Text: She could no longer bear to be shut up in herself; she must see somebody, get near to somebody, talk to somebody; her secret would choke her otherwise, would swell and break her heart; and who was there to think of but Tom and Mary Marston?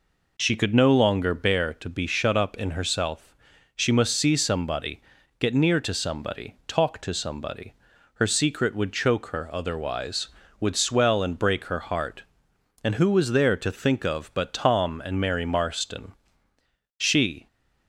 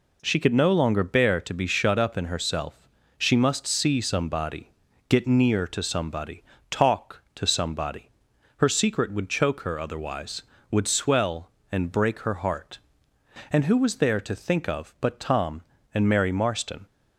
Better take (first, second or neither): second